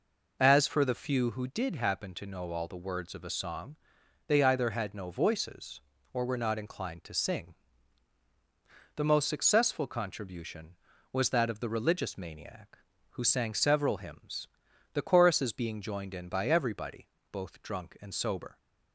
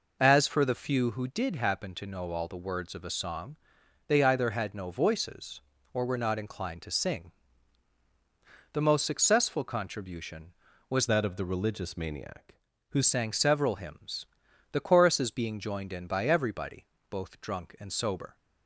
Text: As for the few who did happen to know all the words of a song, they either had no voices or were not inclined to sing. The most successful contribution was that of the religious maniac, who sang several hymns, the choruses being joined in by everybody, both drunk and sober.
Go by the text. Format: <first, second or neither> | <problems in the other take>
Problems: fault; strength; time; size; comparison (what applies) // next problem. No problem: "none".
first | changes voice from "that" to "who"; from 11.0 to 13.0 s; 2.0 s long